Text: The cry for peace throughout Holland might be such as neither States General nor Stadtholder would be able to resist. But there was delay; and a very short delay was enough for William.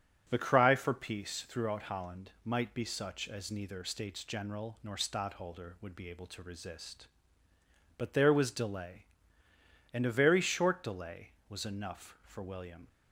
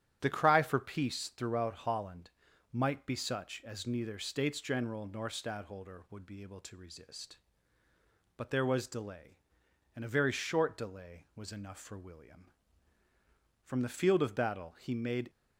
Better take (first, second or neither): first